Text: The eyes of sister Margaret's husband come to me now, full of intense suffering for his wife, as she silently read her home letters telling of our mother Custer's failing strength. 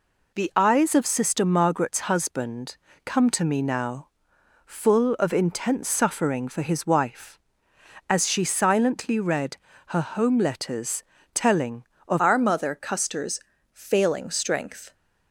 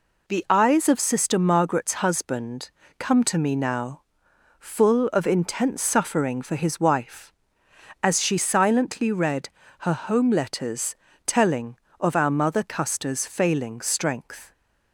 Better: second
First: pauses between "husband" and "come"; slight; at 2.7 s; 0.28 s long // pauses between "read" and "her"; slight; at 9.5 s; 0.30 s long // pauses between "letters" and "telling"; slight; at 11.0 s; 0.32 s long // changes voice at "our"; from 12.1 s on; 2.8 s long // pauses between "Custer's" and "failing"; slight; at 13.4 s; 0.32 s long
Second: pauses between "husband" and "come"; slight; at 2.7 s; 0.28 s long // pauses between "read" and "her"; slight; at 9.4 s; 0.30 s long // pauses between "letters" and "telling"; slight; at 10.9 s; 0.32 s long

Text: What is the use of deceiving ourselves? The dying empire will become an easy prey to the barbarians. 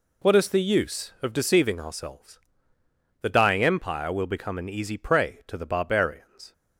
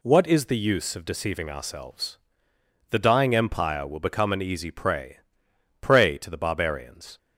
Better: first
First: none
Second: says "prey" twice; at 5.7 s

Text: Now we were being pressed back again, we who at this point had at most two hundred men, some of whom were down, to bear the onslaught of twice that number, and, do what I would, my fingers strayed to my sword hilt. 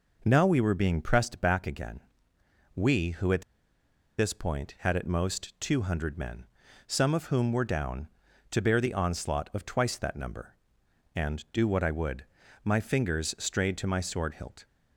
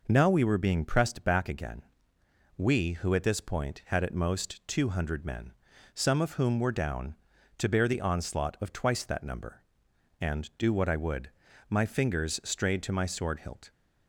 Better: second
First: pauses between "at" and "this"; noticeable; at 3.4 s; 0.77 s long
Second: none

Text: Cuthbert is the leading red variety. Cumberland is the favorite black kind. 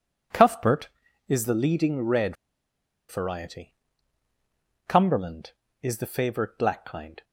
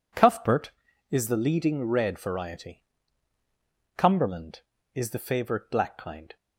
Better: second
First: pauses between "red" and "variety"; noticeable; at 2.3 s; 0.74 s long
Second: none

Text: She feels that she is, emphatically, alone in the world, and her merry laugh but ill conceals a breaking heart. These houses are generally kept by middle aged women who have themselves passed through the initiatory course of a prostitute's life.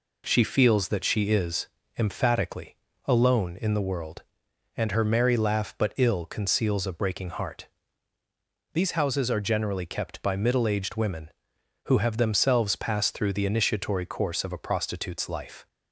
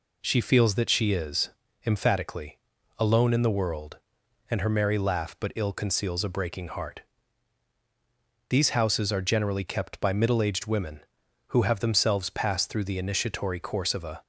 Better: first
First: none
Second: stops before "prostitute's life"; at 14.2 s

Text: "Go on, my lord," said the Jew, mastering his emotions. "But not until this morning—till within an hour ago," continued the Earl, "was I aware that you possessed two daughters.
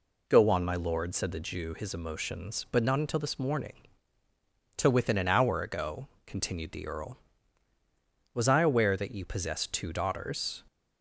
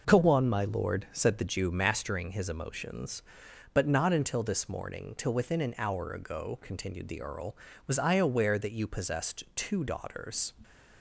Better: second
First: skips "mastering"; at 1.7 s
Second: none

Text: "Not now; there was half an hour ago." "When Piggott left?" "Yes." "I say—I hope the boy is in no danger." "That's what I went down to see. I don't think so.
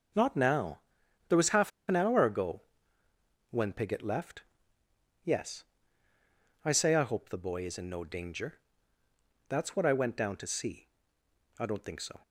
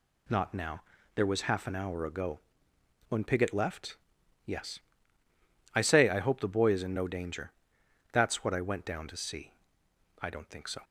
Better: second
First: starts louder than the rest; noticeable; until 1.6 s; 6 dB // pauses between "half" and "an"; slight; at 1.7 s; 0.17 s long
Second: none

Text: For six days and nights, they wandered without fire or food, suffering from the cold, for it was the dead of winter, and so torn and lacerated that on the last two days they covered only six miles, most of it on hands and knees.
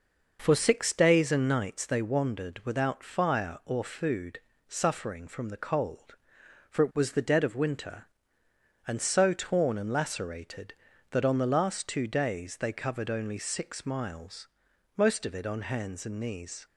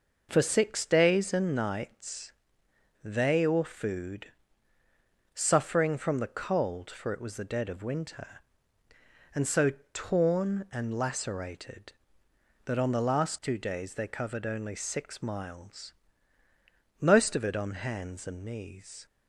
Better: first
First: none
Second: skips "wandered without fire"; at 3.4 s // pauses between "so" and "torn"; slight; at 9.7 s; 0.20 s long

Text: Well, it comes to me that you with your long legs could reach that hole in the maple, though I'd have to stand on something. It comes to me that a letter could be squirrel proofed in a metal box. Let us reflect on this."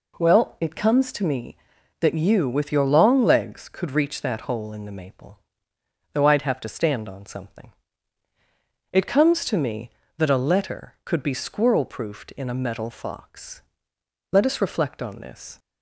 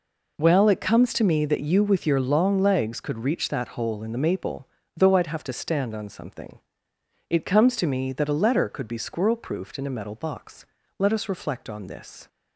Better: second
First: says "fox" for "box"; at 12.9 s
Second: none

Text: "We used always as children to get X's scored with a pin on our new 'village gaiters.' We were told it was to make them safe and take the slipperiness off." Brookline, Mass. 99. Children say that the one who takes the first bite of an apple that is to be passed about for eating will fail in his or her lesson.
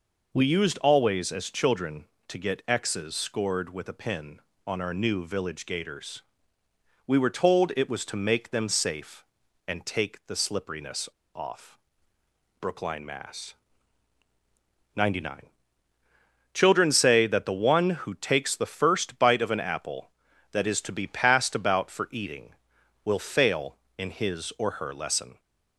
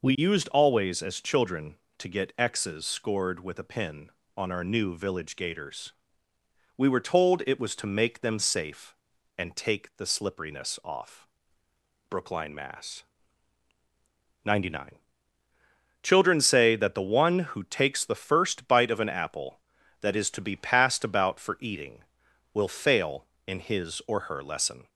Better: second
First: pauses between "slipperiness" and "off"; slight; at 11.0 s; 0.24 s long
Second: none

